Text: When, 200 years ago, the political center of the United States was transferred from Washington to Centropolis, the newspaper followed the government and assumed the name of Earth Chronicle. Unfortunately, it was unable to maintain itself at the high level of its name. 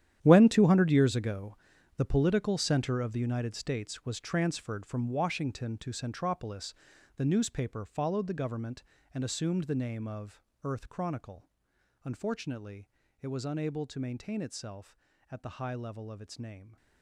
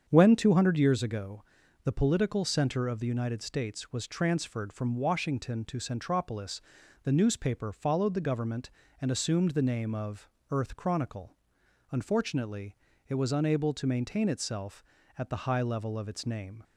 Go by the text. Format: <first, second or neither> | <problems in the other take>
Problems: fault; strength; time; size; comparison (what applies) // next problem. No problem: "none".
second | gets quieter; strong; throughout; 13.5 dB // starts louder than the rest; strong; until 1.2 s; 10.5 dB; strong in the second // pauses between "of" and "Earth"; slight; at 10.4 s; 0.20 s long; slight in the second